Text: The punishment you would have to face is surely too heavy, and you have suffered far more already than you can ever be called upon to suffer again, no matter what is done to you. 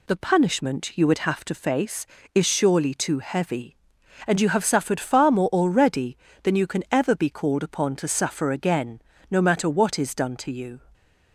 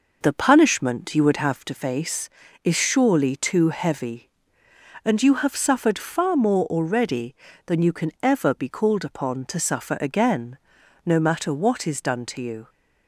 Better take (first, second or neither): first